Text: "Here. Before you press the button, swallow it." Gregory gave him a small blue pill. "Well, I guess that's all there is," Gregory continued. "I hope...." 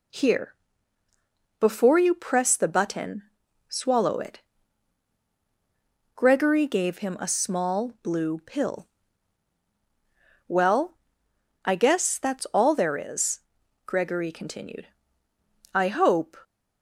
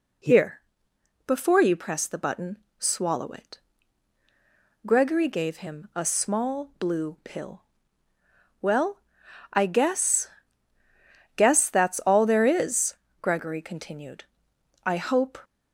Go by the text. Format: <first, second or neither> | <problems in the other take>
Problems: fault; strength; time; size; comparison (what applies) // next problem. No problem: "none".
first | says "guess" twice; at 11.3 s